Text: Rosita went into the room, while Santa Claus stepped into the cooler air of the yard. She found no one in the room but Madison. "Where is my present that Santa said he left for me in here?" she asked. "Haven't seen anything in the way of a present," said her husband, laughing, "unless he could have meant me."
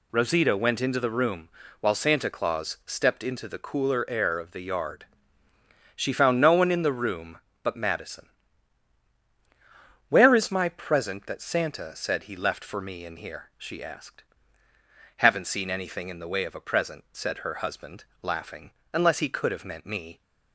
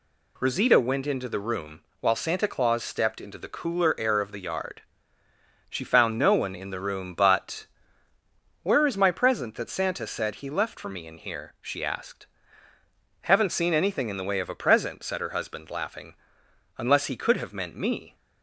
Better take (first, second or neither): first